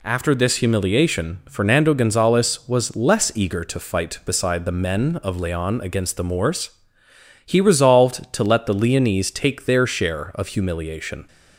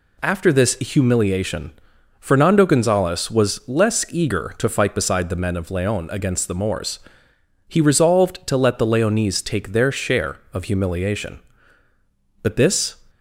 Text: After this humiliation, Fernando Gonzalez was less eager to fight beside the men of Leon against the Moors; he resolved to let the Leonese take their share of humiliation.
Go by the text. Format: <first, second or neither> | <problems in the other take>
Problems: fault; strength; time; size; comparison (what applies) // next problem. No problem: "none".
first | goes on to say "But this"; from 12.4 s on; 0.54 s long